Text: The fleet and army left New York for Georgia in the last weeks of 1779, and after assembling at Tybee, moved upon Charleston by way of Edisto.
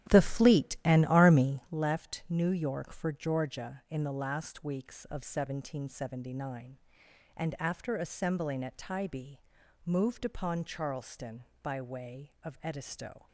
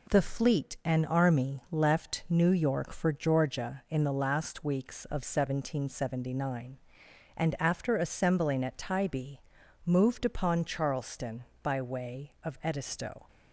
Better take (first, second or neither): second